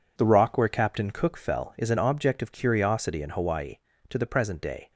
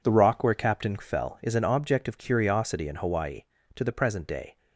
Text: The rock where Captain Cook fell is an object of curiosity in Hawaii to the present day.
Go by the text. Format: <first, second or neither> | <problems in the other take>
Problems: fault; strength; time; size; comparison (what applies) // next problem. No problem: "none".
first | skips "Cook"; at 0.9 s